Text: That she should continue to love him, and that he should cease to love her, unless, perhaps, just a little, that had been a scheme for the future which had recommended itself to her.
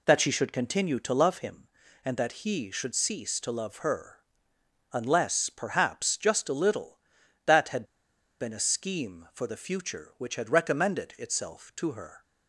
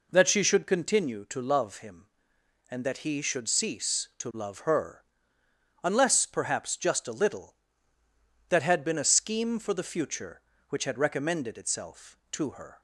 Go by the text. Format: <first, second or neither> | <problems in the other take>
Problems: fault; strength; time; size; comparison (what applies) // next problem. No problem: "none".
second | pauses between "had" and "been"; noticeable; at 7.8 s; 0.54 s long